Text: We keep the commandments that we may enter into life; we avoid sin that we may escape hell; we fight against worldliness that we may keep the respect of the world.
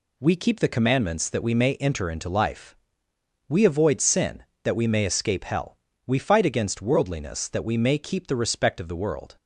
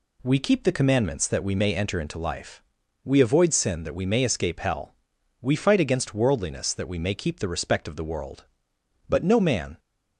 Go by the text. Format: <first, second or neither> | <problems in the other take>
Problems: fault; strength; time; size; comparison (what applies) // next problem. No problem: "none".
first | goes on to say "But no man"; noticeable; from 9.0 s on; 0.70 s long